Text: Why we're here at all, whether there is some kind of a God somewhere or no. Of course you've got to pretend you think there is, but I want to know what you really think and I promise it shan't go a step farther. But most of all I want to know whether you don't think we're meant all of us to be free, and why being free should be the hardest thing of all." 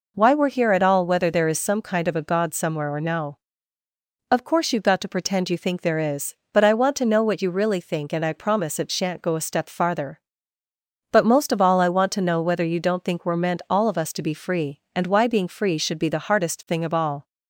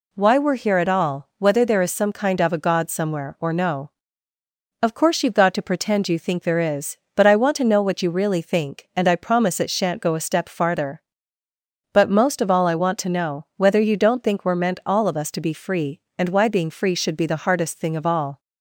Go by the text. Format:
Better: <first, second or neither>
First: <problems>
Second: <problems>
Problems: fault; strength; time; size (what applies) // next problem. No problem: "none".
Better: neither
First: none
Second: none